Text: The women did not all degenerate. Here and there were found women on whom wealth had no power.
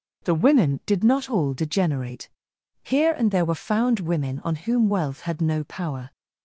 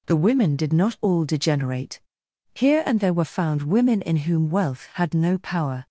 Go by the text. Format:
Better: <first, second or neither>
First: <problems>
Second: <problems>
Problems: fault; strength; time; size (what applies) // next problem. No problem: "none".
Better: first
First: none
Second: says "in" for "on"; at 4.0 s